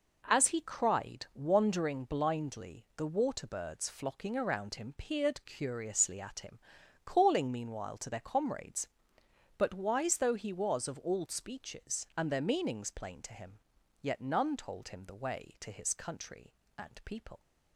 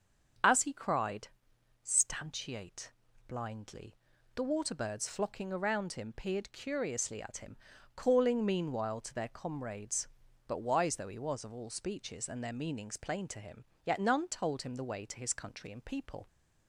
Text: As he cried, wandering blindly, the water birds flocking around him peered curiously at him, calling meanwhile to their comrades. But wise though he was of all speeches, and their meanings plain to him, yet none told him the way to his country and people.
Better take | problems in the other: first | starts louder than the rest; until 1.9 s; 6.5 dB // says "stantiate" for "wandering"; at 1.8 s

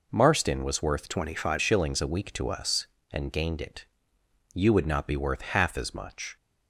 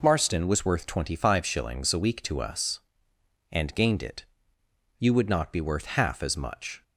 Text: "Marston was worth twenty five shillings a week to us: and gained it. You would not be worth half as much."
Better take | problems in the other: second | changes voice from "twenty" to "five"; from 1.0 to 1.6 s; 0.6 s long

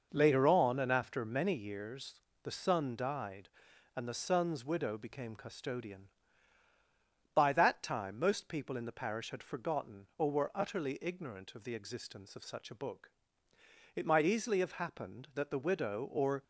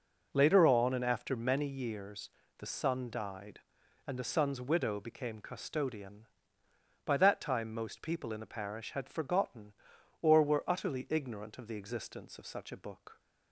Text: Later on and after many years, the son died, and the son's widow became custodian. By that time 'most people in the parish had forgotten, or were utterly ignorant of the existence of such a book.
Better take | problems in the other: second | goes on to say "It might easily have happened that the widow or"; strong; from 13.9 s on; 2.4 s long

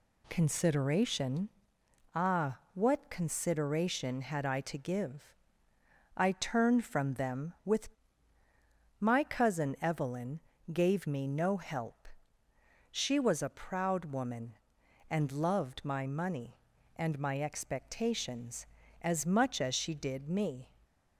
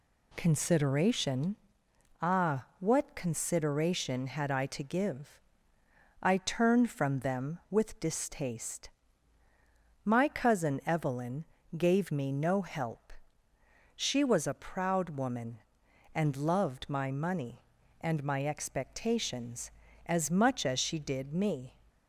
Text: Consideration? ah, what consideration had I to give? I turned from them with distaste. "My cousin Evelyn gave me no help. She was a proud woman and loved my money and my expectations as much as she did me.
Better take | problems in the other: second | skips "distaste"; at 8.4 s // pauses between "Evelyn" and "gave"; slight; at 10.4 s; 0.32 s long; slight in the second

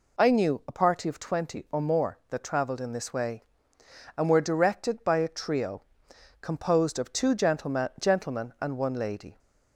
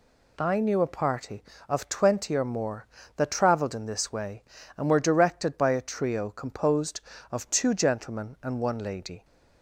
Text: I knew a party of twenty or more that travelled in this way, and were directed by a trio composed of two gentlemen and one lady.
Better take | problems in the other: second | pauses between "trio" and "composed"; noticeable; at 5.8 s; 0.58 s long // says "gentlemen" twice; at 8.0 s

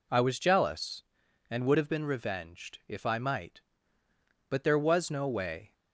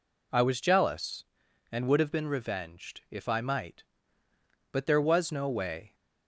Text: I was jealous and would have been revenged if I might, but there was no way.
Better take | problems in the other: neither | none

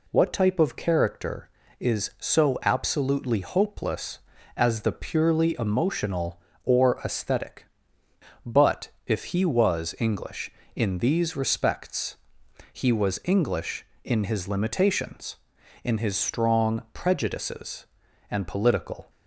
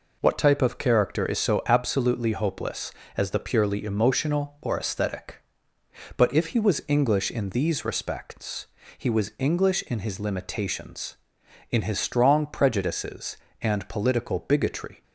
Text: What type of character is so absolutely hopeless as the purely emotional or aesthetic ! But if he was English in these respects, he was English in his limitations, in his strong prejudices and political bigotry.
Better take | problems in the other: second | pauses between "But" and "if"; slight; at 8.8 s; 0.16 s long // stops before "bigotry"; at 19.0 s

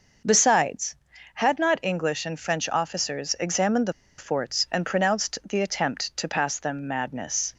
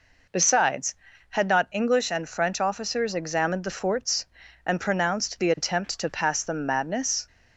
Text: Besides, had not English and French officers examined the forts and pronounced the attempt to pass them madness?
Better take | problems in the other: second | pauses between "the" and "forts"; slight; at 3.9 s; 0.26 s long

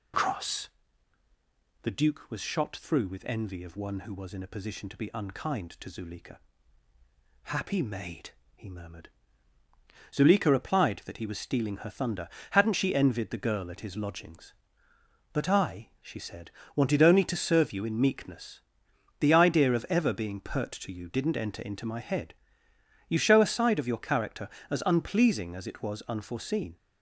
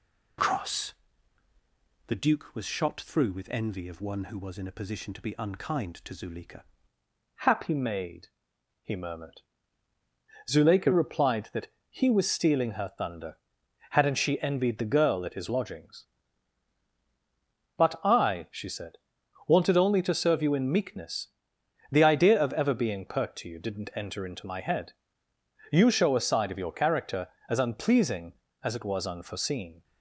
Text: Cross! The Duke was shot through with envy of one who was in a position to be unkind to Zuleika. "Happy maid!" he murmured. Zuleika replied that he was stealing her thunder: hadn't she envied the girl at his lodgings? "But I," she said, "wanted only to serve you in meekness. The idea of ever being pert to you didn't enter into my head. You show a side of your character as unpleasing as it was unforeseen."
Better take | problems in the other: first | changes voice at "Happy"; from 7.3 s on; 22.5 s long // pauses between "that" and "he"; slight; at 11.6 s; 0.22 s long

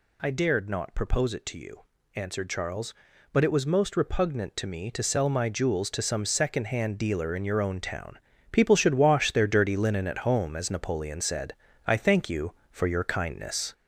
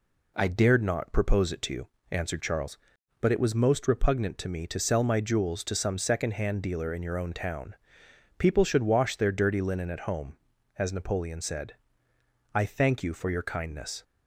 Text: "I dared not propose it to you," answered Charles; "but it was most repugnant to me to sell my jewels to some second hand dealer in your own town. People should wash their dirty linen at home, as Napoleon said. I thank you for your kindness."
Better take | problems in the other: second | gets louder; throughout; 3.5 dB

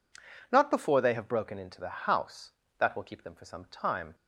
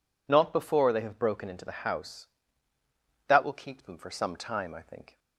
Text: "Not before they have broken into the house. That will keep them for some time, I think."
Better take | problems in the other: second | stops before "I think"; at 4.1 s

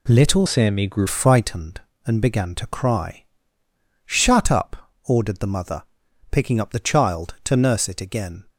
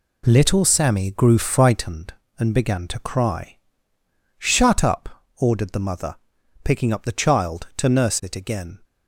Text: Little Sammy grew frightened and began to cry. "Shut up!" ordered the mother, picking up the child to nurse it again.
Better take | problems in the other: second | changes voice from "Sammy" to "grew"; from 0.4 to 1.0 s; 0.6 s long

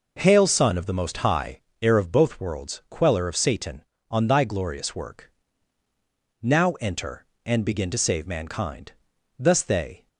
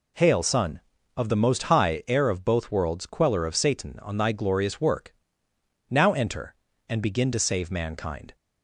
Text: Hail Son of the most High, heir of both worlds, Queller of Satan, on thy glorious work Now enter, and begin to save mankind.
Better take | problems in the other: second | pauses between "work" and "Now"; at 5.3 s; 1.1 s long; noticeable in the second // goes on to say "Thus they"; noticeable; from 9.3 s on; 0.70 s long

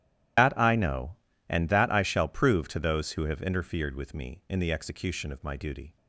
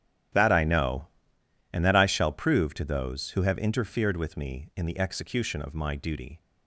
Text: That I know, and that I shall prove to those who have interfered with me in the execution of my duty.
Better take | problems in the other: second | loses the start of "That"; at 0.3 s; 135 ms // starts louder than the rest; strong; until 1.7 s; 12 dB; strong in the second

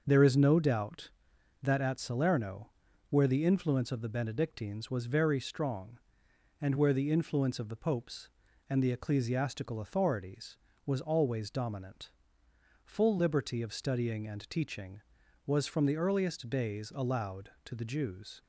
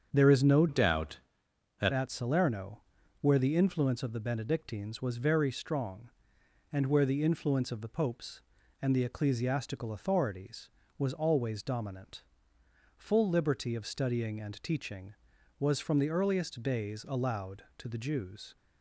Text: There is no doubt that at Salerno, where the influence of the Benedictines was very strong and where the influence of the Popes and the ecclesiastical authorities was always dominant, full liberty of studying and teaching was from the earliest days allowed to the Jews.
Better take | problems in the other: first | starts louder than the rest; strong; until 1.1 s; 7.5 dB; also in the first // changes voice from "doubt" to "that"; from 0.6 to 1.9 s; 1.3 s long

